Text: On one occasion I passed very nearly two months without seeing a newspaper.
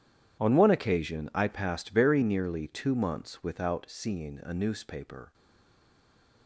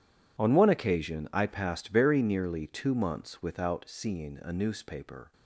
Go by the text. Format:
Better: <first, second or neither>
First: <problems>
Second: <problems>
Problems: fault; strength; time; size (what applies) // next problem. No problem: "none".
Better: second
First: stays silent after the last word; from 5.3 s on; 1.1 s long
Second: none